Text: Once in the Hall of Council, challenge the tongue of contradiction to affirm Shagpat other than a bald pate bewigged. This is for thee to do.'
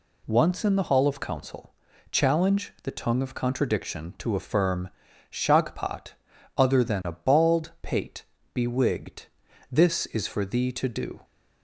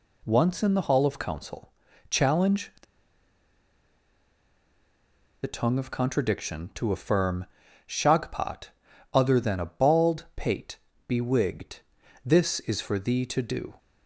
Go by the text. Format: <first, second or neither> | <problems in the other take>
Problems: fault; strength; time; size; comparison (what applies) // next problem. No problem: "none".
first | pauses between "the" and "tongue"; strong; at 2.8 s; 2.6 s long // pauses between "affirm" and "Shagpat"; at 7.4 s; 0.42 s long; also in the first // pauses between "Shagpat" and "other"; at 8.6 s; 0.44 s long; also in the first // pauses between "pate" and "bewigged"; slight; at 10.7 s; 0.28 s long; slight in the first